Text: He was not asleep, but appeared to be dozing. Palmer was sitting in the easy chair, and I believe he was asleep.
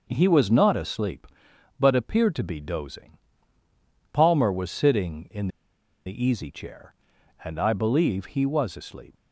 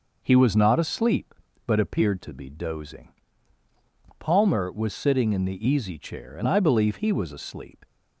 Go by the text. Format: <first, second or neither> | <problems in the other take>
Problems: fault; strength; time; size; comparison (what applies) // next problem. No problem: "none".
second | pauses between "in" and "the"; noticeable; at 5.4 s; 0.57 s long